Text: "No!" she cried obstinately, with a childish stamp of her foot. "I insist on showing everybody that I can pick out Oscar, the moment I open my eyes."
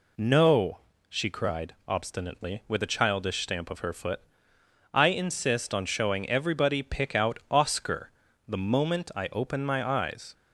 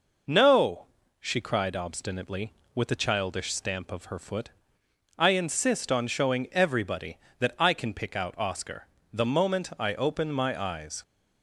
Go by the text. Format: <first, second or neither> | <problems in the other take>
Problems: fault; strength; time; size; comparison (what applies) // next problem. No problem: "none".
second | skips "that I can"; at 6.8 s